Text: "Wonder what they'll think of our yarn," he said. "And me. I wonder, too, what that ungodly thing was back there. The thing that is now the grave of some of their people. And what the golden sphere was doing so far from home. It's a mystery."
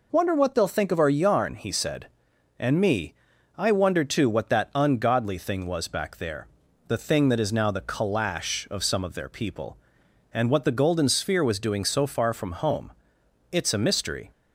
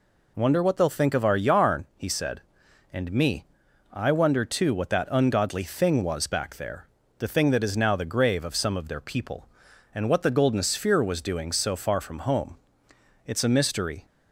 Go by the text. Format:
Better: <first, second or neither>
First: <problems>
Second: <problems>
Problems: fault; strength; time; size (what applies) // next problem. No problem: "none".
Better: second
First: says "calash" for "grave"; at 7.8 s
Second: none